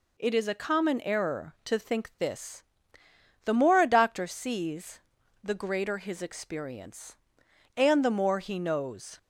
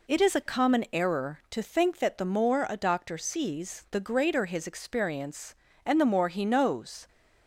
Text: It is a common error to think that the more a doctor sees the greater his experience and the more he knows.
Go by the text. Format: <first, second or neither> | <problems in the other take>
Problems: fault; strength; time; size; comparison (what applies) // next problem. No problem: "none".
second | says "this" for "that"; at 2.1 s // pauses between "sees" and "the"; at 4.9 s; 0.42 s long